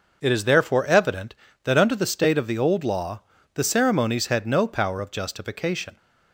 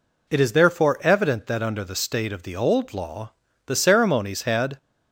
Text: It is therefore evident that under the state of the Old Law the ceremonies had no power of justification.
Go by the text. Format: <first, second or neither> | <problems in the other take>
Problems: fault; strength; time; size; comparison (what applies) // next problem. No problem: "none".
first | pauses between "Law" and "the"; slight; at 3.3 s; 0.33 s long; slight in the first // stops before "no power of justification"; at 4.7 s